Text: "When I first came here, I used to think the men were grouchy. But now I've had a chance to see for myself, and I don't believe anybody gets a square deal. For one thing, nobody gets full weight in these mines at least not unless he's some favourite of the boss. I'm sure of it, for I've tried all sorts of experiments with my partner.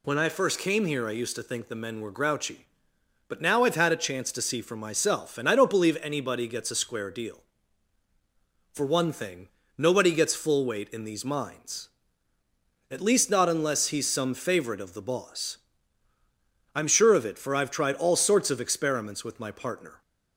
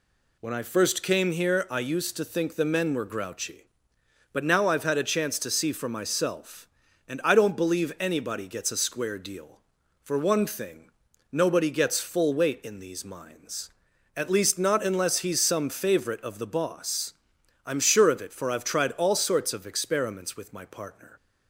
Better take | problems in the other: neither | none

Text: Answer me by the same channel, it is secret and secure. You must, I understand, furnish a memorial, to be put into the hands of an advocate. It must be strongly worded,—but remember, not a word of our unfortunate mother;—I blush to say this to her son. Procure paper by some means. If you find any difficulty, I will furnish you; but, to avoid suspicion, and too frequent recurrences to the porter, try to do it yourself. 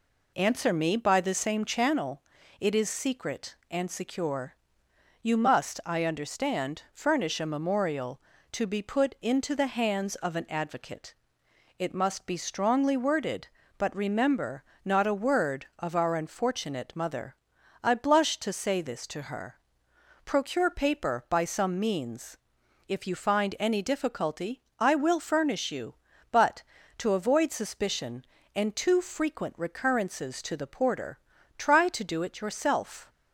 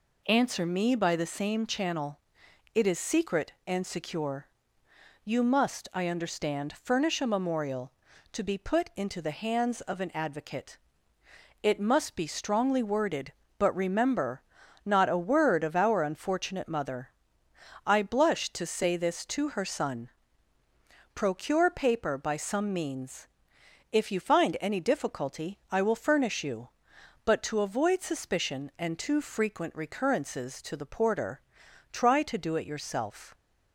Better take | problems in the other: second | skips "son"; at 19.9 s

